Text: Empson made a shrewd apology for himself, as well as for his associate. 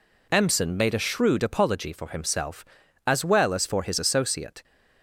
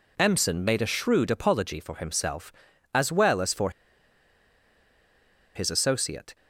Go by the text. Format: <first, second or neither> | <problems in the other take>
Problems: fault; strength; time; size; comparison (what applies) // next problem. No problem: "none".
first | pauses between "for" and "his"; strong; at 3.7 s; 1.8 s long